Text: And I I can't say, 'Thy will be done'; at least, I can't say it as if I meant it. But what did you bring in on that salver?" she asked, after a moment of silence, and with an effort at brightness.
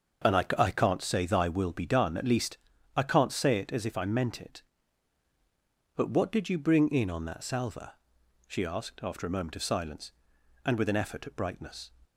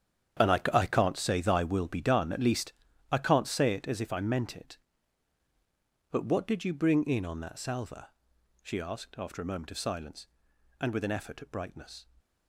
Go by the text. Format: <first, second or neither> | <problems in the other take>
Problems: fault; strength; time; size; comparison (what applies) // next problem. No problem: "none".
first | gets quieter; strong; throughout; 13.5 dB // starts louder than the rest; strong; until 1.5 s; 9 dB; also in the first